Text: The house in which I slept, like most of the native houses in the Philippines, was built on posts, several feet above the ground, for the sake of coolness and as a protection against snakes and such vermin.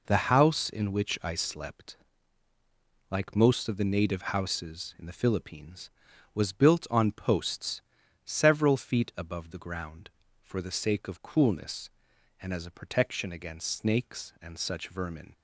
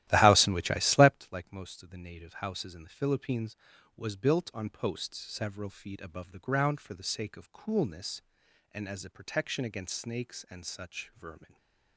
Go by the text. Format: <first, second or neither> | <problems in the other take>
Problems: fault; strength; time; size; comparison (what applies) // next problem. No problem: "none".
first | starts louder than the rest; strong; until 1.1 s; 14 dB // stays silent after the last word; slight; from 11.4 s on; 0.5 s long